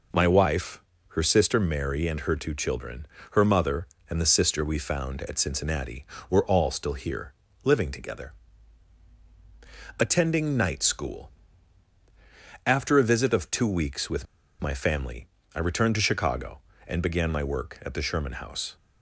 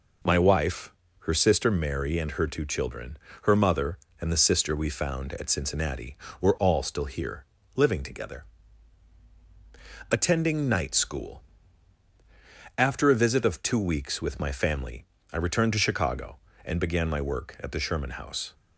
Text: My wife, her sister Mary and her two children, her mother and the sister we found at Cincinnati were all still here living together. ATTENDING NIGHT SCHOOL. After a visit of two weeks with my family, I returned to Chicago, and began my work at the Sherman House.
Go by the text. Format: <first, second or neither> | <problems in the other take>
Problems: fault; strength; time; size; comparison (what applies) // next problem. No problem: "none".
second | pauses between "here" and "living"; slight; at 7.3 s; 0.30 s long; slight in the second // pauses between "with" and "my"; at 14.2 s; 0.36 s long